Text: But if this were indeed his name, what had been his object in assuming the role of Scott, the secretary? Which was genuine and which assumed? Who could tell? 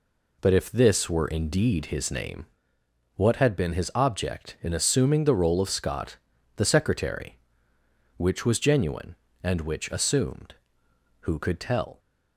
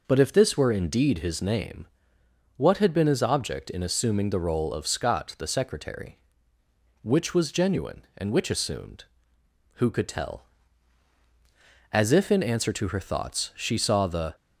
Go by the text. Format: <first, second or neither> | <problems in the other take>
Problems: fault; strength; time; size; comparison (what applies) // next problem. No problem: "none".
first | goes on to say "As if in answer to her thoughts she saw the"; strong; from 11.9 s on; 2.4 s long